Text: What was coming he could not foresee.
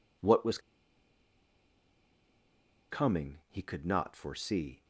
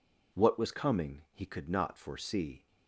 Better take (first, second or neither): second